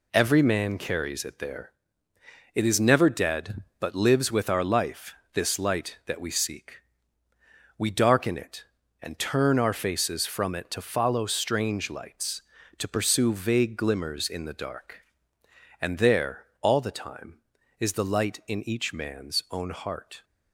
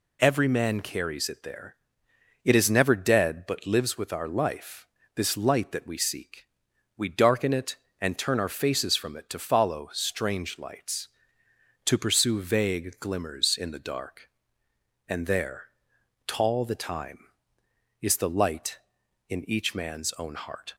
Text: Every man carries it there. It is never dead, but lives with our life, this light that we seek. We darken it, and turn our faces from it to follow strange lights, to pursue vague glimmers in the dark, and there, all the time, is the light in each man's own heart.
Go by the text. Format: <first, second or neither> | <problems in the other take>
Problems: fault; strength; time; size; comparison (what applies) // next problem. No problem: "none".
first | says "tall" for "all"; at 16.2 s